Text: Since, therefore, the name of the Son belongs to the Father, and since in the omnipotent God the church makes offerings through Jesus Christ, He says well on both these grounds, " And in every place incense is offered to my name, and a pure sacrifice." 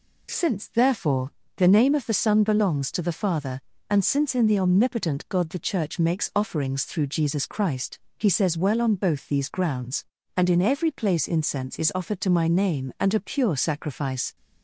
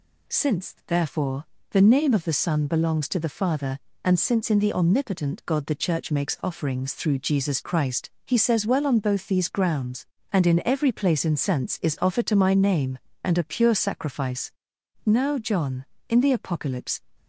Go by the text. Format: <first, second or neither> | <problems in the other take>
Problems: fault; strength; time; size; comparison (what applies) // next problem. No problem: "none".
first | goes on to say "Now John in the Apocalypse"; strong; from 15.0 s on; 1.9 s long